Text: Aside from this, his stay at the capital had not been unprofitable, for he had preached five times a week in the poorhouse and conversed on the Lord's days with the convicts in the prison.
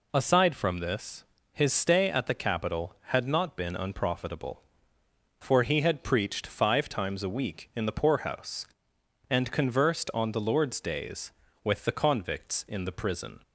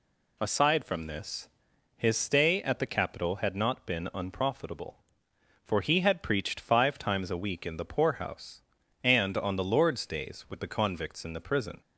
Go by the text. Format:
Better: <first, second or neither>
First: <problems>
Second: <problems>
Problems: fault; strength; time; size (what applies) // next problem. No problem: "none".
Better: first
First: none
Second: skips "conversed"; at 9.3 s